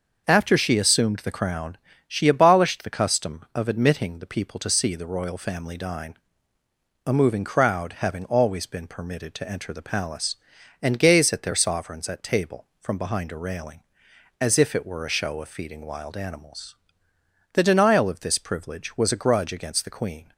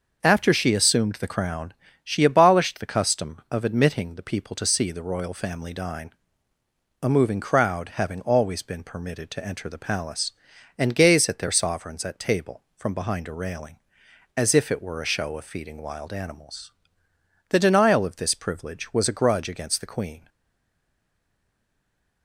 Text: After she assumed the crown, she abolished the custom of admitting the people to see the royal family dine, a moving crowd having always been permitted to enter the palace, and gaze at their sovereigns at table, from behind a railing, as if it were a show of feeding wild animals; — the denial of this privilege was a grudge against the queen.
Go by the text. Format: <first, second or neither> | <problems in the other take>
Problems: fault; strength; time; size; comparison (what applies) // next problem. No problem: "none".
first | starts louder than the rest; until 1.2 s; 6 dB; also in the first // stays silent after the last word; noticeable; from 20.2 s on; 2.0 s long